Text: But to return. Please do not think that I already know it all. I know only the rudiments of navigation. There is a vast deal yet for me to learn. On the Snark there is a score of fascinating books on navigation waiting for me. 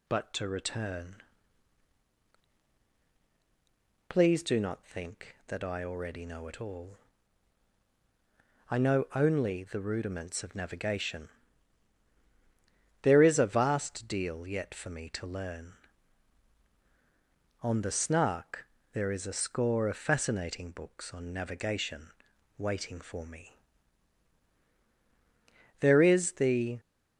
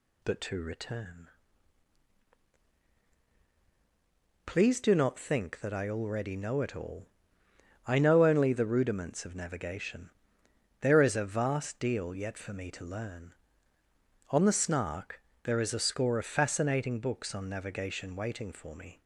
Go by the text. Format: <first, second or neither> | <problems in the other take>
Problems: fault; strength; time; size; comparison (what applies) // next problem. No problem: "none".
second | pauses between "Snark" and "there"; slight; at 18.6 s; 0.28 s long; slight in the second // pauses between "navigation" and "waiting"; noticeable; at 22.0 s; 0.50 s long // goes on to say "There is the"; noticeable; from 25.8 s on; 0.98 s long